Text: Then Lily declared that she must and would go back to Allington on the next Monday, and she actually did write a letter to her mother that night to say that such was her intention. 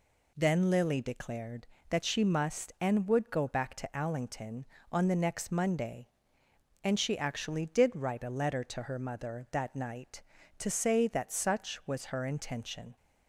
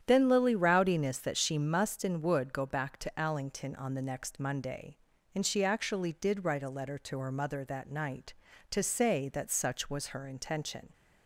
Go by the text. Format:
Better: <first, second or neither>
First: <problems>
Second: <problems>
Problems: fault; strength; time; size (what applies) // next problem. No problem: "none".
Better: first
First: none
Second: starts louder than the rest; strong; until 1.0 s; 9.5 dB // says "rowdiness" for "declared"; at 0.5 s